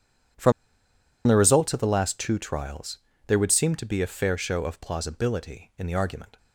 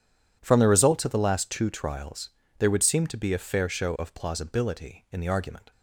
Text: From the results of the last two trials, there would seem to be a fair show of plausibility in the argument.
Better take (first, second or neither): second